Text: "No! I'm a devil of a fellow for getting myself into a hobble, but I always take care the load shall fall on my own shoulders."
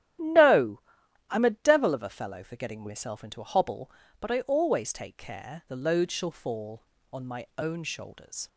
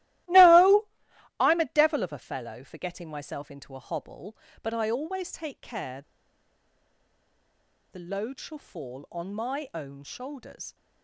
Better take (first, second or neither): first